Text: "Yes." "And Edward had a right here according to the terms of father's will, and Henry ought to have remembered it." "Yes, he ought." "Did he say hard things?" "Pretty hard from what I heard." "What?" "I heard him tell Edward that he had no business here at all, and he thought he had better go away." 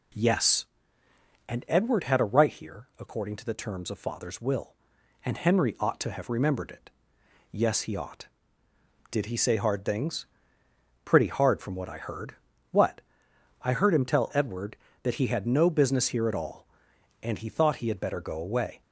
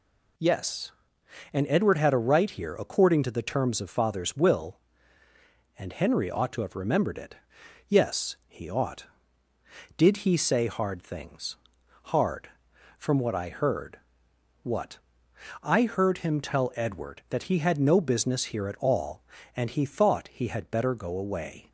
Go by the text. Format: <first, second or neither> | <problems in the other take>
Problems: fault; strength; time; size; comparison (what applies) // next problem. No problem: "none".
first | skips "Pretty"; at 11.8 s